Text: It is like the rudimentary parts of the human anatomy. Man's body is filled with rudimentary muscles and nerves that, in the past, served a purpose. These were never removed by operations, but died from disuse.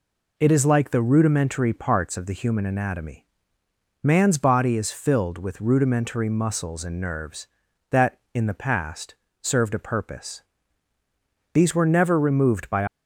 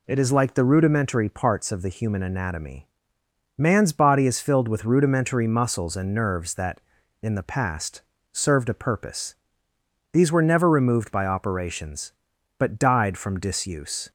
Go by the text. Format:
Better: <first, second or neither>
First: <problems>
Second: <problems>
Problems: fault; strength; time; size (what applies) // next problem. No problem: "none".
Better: second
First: stops before "operations but died from disuse"; at 12.8 s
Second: none